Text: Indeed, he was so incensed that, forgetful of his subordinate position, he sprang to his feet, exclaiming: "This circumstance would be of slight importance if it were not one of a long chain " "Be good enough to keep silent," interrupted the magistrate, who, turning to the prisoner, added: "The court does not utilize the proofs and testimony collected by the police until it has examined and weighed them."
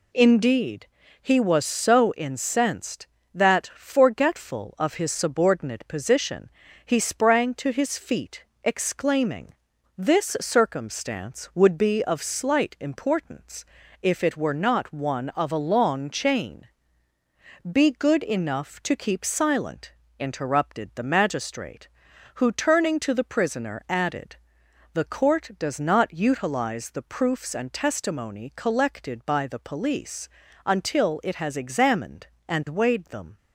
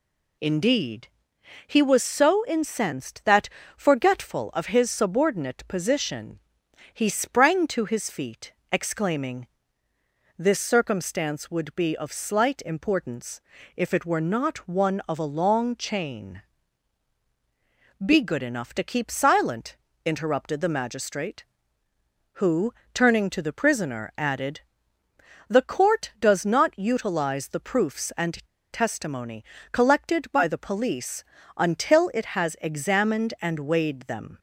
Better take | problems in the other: first | pauses between "importance" and "if"; slight; at 13.4 s; 0.36 s long; also in the first // pauses between "and" and "testimony"; slight; at 28.4 s; 0.28 s long // pauses between "testimony" and "collected"; slight; at 29.4 s; 0.28 s long // pauses between "police" and "until"; slight; at 31.2 s; 0.32 s long; also in the first

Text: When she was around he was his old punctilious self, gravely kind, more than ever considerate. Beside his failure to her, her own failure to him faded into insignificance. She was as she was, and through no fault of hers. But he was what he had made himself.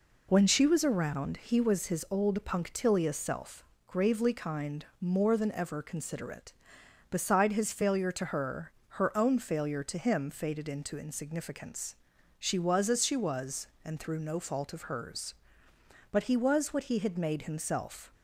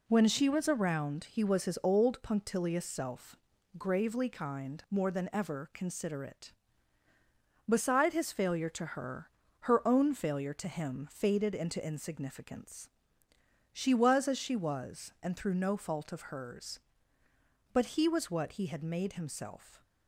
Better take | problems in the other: neither | none

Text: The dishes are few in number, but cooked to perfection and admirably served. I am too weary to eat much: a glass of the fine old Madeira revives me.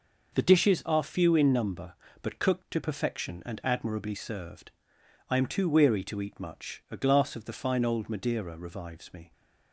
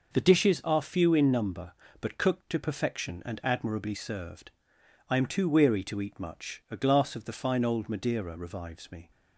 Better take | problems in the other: neither | none

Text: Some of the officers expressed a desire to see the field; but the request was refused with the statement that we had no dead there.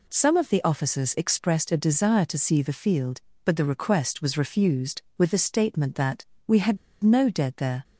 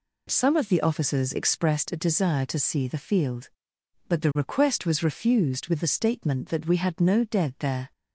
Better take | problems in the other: second | pauses between "that" and "we"; slight; at 6.2 s; 0.22 s long // pauses between "had" and "no"; slight; at 6.7 s; 0.26 s long

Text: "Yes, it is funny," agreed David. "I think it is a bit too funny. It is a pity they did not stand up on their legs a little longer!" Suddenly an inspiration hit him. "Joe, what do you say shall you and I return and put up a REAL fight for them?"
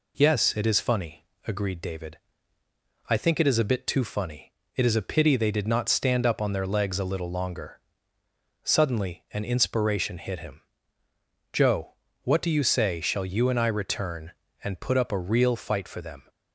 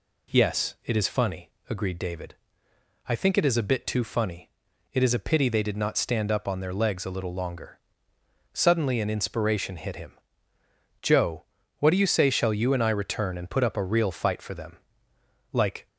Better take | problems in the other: first | goes on to say "Like"; slight; from 15.5 s on; 0.36 s long

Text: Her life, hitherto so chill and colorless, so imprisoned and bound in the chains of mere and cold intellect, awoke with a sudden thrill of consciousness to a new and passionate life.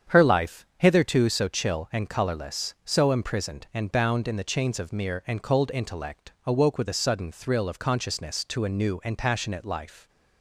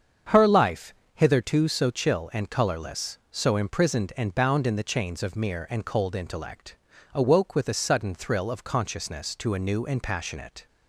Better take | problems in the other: first | starts louder than the rest; strong; until 1.5 s; 7 dB; strong in the first // stops before "life"; at 10.6 s

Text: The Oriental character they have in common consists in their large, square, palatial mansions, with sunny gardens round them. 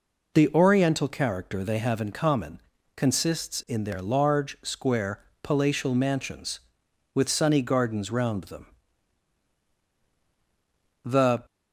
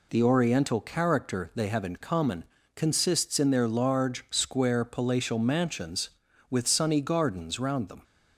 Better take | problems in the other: second | pauses between "common" and "consists"; slight; at 2.6 s; 0.34 s long; slight in the second // goes on to say "The"; slight; from 11.0 s on; 0.38 s long

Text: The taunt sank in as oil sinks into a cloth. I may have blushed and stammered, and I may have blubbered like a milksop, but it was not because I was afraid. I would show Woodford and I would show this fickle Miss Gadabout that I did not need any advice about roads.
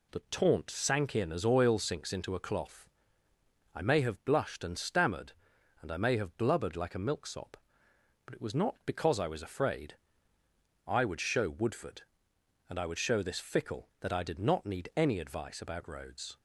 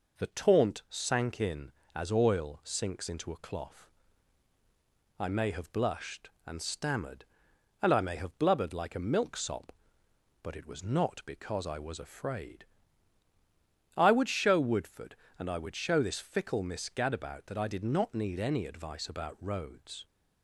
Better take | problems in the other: second | skips "Miss Gadabout"; at 13.9 s

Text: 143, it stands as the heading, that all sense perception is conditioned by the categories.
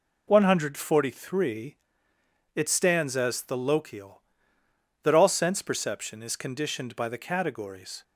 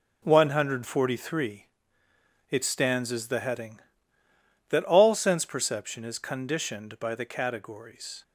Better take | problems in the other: second | says "lochial" for "heading"; at 3.5 s

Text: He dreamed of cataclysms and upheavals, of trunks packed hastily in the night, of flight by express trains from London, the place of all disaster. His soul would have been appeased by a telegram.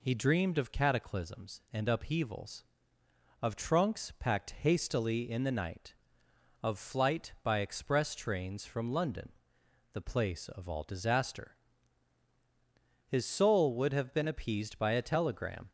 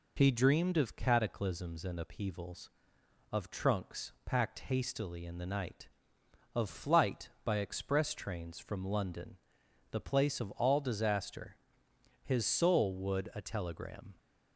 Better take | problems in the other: first | skips "have been appeased by"; at 13.3 s

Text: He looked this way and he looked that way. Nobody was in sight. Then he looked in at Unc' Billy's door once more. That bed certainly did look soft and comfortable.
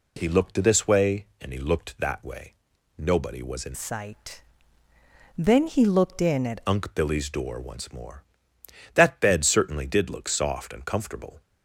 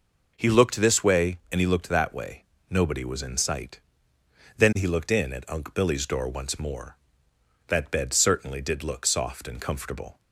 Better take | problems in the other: second | changes voice from "sight" to "at"; from 3.7 to 6.5 s; 2.8 s long

